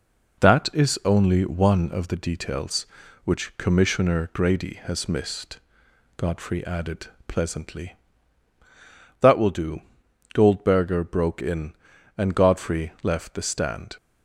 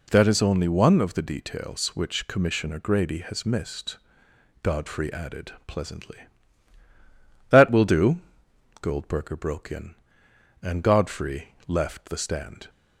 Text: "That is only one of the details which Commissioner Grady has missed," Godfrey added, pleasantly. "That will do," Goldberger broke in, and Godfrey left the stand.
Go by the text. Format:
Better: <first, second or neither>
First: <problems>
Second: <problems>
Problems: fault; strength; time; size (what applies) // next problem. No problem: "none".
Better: neither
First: none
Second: none